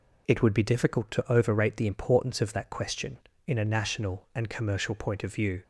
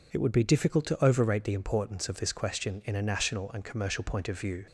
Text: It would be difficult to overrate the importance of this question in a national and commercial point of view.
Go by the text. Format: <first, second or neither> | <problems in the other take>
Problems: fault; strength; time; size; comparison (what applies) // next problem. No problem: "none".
second | says "that" for "this"; at 2.5 s